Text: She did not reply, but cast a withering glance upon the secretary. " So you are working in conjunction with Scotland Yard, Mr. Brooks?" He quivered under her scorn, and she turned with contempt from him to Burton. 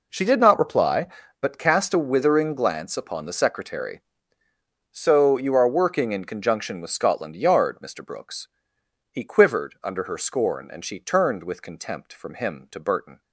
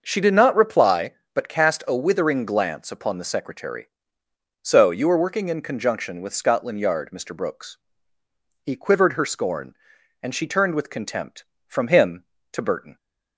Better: first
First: none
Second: starts louder than the rest; until 1.0 s; 6 dB // skips "under"; at 9.1 s

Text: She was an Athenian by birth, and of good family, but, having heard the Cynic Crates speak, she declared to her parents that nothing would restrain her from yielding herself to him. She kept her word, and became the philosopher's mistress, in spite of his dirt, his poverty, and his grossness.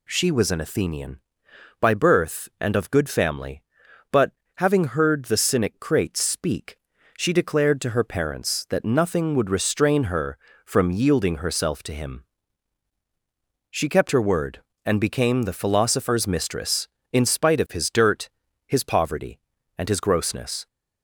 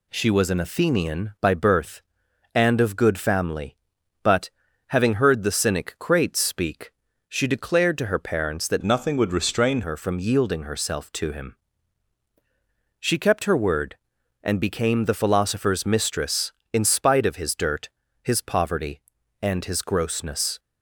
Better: first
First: none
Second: changes voice from "nothing" to "restrain"; from 8.8 to 9.8 s; 1.0 s long

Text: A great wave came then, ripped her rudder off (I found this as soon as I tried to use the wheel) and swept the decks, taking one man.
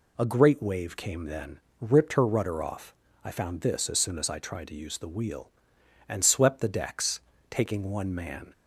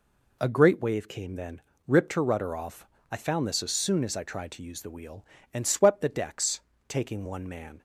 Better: neither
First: none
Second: none

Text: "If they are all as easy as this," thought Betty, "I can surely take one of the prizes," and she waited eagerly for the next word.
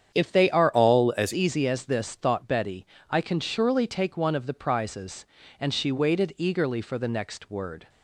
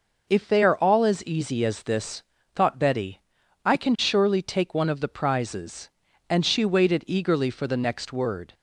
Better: second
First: starts louder than the rest; strong; until 1.2 s; 8.5 dB // changes voice from "all" to "as"; from 0.7 to 1.3 s; 0.6 s long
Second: none

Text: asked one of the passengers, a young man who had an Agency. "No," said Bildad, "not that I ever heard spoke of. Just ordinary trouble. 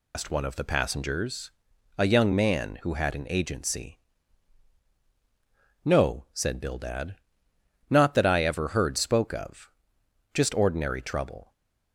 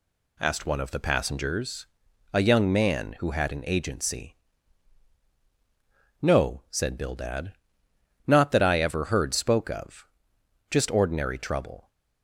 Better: second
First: loses the start of "asked"; at 0.1 s; 110 ms // stays silent after the last word; slight; from 11.4 s on; 0.5 s long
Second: none

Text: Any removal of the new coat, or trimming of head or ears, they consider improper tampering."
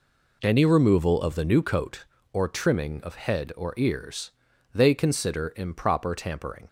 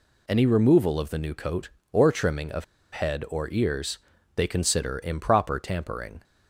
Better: first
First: none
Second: pauses between "of" and "head"; slight; at 2.6 s; 0.28 s long

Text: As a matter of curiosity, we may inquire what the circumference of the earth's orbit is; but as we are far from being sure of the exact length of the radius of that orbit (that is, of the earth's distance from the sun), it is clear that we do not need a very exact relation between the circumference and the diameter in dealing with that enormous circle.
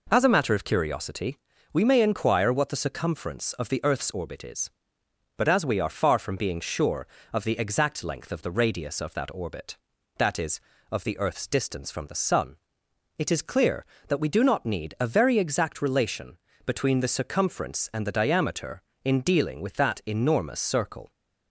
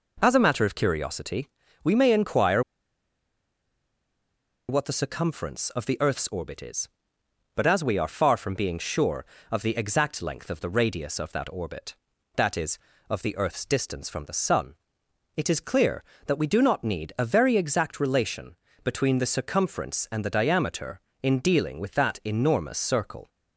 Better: first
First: pauses between "relation" and "between"; slight; at 16.3 s; 0.28 s long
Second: pauses between "inquire" and "what"; strong; at 2.6 s; 2.0 s long // pauses between "relation" and "between"; slight; at 18.5 s; 0.28 s long

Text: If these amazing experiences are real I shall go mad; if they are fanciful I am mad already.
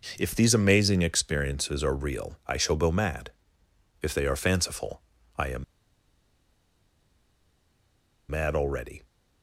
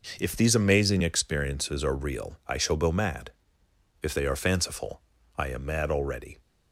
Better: second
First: pauses between "fanciful" and "I"; slight; at 5.0 s; 0.34 s long // pauses between "am" and "mad"; strong; at 5.6 s; 2.6 s long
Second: pauses between "fanciful" and "I"; slight; at 5.0 s; 0.34 s long

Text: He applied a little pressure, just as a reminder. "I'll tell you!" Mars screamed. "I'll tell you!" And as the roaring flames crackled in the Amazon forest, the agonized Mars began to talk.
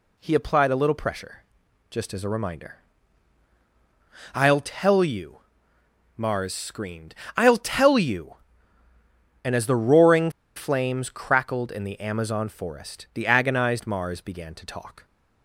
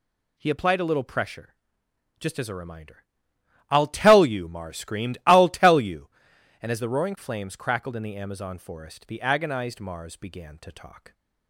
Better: second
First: pauses between "roaring" and "flames"; slight; at 10.3 s; 0.25 s long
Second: none

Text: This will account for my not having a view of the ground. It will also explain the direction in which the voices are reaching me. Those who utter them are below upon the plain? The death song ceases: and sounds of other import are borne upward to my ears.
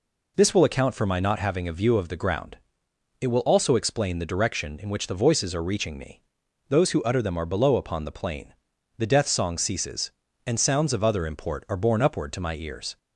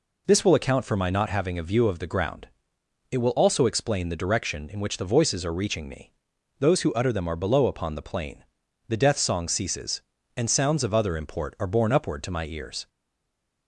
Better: first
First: none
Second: stays silent after the last word; slight; from 12.8 s on; 0.8 s long

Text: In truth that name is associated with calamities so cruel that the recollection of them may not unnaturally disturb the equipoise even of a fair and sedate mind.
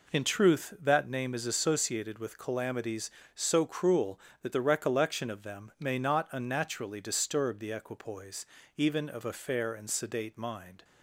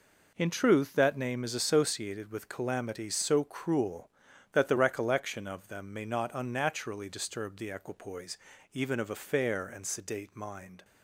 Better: neither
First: pauses between "equipoise" and "even"; slight; at 8.4 s; 0.30 s long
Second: pauses between "equipoise" and "even"; slight; at 8.3 s; 0.34 s long

